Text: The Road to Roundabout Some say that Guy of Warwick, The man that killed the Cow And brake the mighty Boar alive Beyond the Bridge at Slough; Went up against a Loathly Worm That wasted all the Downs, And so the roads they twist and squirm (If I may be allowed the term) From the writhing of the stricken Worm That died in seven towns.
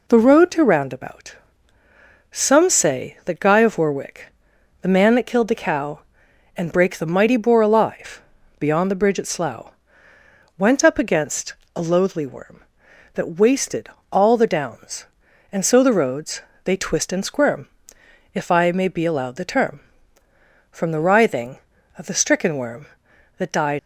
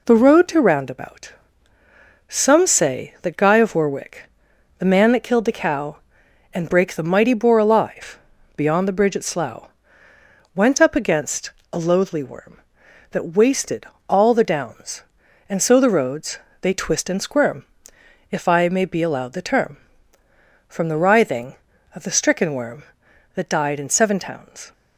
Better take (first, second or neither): second